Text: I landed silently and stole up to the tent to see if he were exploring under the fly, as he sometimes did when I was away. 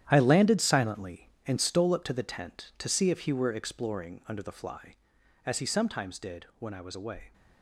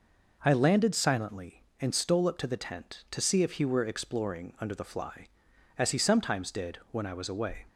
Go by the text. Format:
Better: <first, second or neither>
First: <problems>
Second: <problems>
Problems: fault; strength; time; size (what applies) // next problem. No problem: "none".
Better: second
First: gets quieter; strong; throughout; 11 dB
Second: none